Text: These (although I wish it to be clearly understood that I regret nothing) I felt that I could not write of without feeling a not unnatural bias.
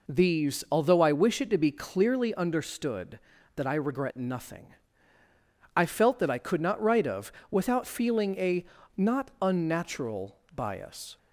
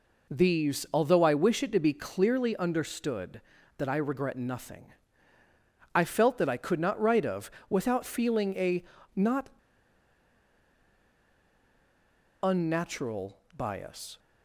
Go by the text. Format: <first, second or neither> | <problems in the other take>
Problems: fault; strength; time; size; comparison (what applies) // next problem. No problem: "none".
first | pauses between "of" and "without"; slight; at 7.4 s; 0.20 s long; slight in the first // pauses between "a" and "not"; slight; at 8.8 s; 0.32 s long; slight in the first // pauses between "not" and "unnatural"; strong; at 9.4 s; 2.9 s long // pauses between "unnatural" and "bias"; slight; at 13.3 s; 0.20 s long; slight in the first